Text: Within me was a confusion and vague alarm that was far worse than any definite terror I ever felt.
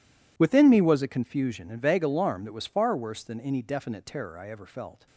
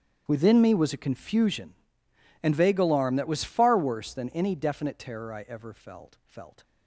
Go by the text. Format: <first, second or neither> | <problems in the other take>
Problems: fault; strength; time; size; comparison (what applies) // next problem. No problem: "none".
first | starts louder than the rest; strong; until 1.2 s; 9 dB // says "felt" twice; at 6.2 s